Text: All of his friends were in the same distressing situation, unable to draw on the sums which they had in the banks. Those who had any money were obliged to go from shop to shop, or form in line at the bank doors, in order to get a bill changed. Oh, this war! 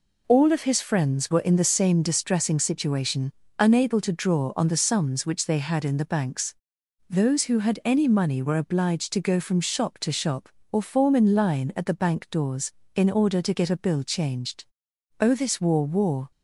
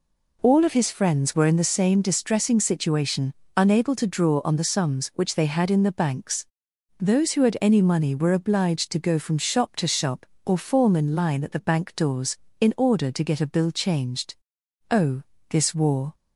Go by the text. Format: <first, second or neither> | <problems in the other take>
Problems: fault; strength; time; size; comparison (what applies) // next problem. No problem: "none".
second | says "war" twice; at 15.8 s